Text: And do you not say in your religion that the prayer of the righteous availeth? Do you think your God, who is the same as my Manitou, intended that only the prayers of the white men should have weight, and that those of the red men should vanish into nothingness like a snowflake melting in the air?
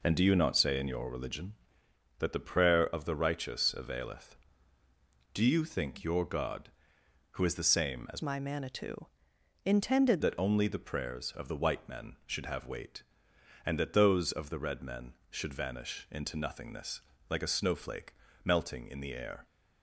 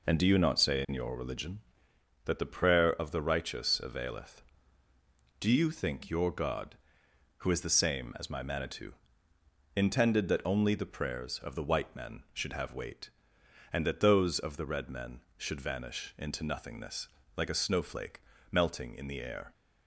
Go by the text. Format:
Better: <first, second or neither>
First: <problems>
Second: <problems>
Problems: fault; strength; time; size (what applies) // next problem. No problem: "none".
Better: second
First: changes voice from "my" to "intended"; from 8.2 to 10.2 s; 2.0 s long // pauses between "nothingness" and "like"; slight; at 17.0 s; 0.28 s long // pauses between "snowflake" and "melting"; slight; at 18.1 s; 0.30 s long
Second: pauses between "nothingness" and "like"; slight; at 17.0 s; 0.28 s long // pauses between "snowflake" and "melting"; slight; at 18.1 s; 0.30 s long